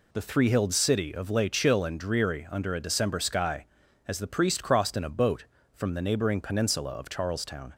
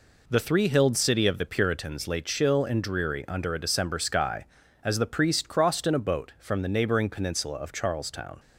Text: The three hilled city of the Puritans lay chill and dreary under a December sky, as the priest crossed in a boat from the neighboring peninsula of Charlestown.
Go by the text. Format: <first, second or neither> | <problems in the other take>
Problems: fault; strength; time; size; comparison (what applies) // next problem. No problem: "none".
second | skips "the Puritans"; at 1.3 s